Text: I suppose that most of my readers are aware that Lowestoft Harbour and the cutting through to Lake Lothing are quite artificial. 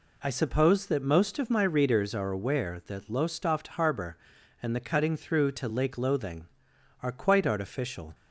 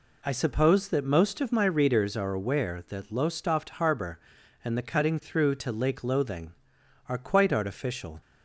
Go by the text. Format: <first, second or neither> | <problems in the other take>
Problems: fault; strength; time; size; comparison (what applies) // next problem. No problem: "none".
neither | none